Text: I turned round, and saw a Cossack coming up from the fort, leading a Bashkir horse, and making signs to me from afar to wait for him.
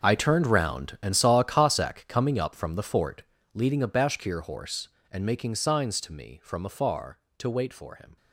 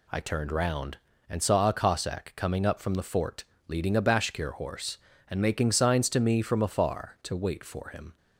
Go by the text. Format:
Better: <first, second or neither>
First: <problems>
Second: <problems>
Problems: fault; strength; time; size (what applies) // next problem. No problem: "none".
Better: second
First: gets quieter; strong; throughout; 14.5 dB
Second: none